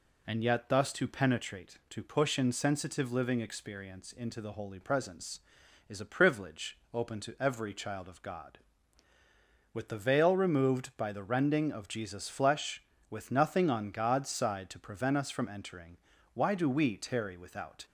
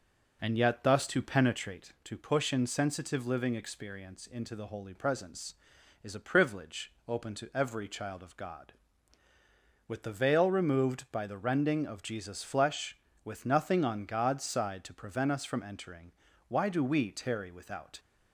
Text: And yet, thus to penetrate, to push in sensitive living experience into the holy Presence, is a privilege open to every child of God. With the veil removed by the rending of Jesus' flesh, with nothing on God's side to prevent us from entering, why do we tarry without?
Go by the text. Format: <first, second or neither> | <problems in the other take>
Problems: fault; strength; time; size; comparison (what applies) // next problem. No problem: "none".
first | starts louder than the rest; noticeable; until 2.1 s; 5 dB // pauses between "privilege" and "open"; slight; at 6.9 s; 0.16 s long; slight in the first